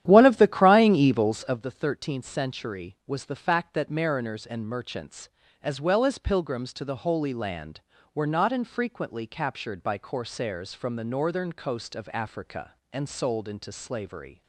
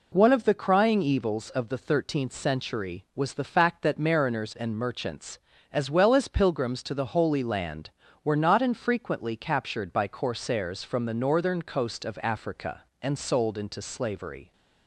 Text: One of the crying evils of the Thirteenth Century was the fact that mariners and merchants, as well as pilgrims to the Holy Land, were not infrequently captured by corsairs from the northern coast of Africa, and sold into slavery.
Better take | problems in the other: second | starts louder than the rest; strong; until 1.7 s; 11.5 dB

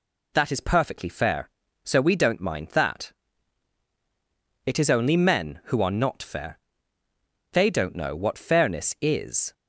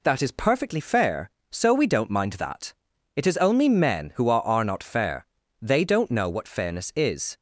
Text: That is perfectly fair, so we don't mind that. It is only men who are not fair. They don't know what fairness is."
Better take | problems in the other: first | says "are" twice; at 4.4 s

